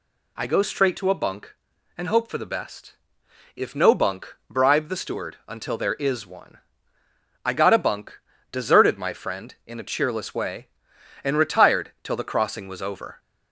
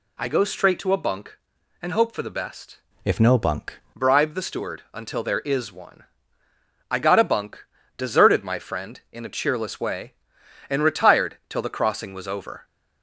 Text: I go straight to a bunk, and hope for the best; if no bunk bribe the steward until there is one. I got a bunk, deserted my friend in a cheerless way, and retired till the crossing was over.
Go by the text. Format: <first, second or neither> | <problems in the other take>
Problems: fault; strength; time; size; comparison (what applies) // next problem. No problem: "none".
first | changes voice from "if" to "bunk"; from 3.0 to 3.7 s; 0.7 s long